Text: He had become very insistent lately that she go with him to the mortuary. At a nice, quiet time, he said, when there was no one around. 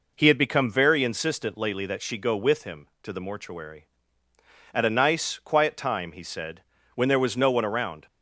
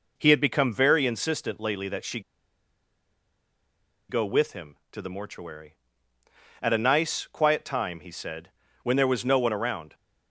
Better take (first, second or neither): first